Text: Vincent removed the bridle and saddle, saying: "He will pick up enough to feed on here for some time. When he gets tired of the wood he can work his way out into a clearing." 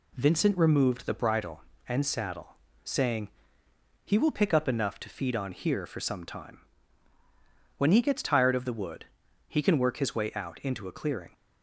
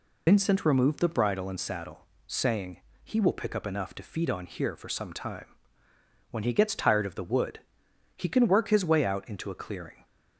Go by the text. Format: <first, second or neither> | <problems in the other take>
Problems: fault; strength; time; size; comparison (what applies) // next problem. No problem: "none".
first | loses the start of "Vincent"; at 0.2 s; 70 ms // pauses between "wood" and "he"; noticeable; at 7.6 s; 0.54 s long; also in the first